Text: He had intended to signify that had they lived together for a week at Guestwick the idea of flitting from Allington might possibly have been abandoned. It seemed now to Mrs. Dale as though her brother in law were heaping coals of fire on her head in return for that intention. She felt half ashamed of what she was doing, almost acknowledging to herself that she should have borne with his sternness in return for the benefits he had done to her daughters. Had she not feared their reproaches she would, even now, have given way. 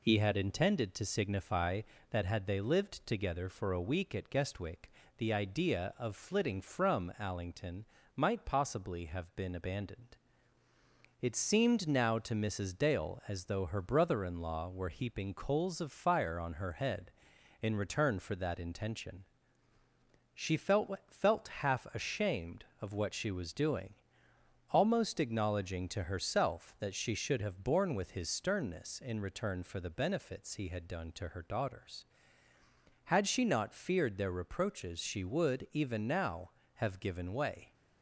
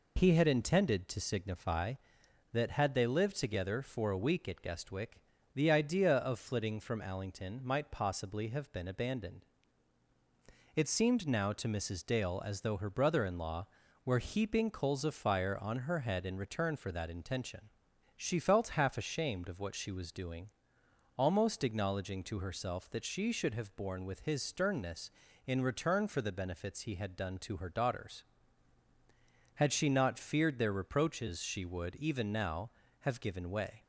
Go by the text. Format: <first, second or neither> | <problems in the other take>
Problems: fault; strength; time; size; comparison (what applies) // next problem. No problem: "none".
second | pauses between "Guestwick" and "the"; slight; at 4.9 s; 0.26 s long; slight in the second // pauses between "Allington" and "might"; slight; at 7.8 s; 0.32 s long // says "felt" twice; at 21.0 s